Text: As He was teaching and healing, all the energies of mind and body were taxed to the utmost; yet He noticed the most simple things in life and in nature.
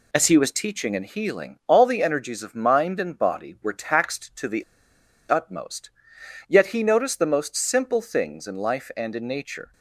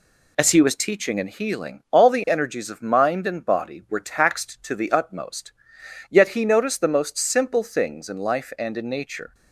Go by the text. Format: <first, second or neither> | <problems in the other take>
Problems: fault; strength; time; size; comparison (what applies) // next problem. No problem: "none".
second | pauses between "the" and "utmost"; noticeable; at 4.6 s; 0.66 s long